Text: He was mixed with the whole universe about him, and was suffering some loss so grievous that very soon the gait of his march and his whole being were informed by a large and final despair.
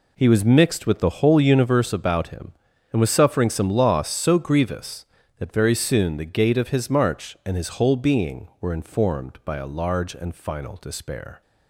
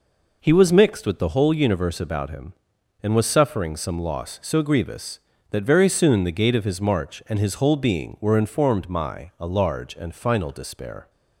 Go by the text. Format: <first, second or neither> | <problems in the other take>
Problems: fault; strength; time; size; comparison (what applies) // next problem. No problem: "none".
first | says "my" for "by"; at 8.8 s